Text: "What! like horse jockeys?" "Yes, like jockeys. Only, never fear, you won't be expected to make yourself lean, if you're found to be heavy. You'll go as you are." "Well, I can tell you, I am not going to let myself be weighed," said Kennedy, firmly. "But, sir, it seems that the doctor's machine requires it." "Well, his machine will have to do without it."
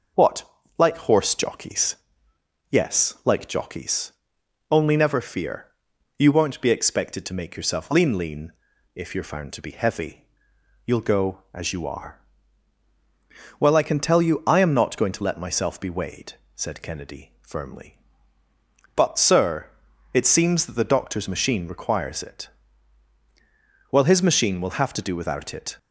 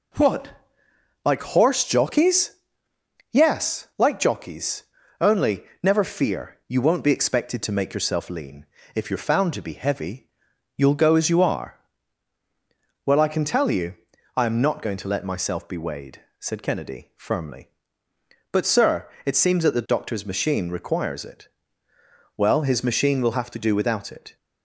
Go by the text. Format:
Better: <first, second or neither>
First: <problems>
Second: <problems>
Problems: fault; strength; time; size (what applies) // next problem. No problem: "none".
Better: second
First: says "lean" twice; at 8.1 s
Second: none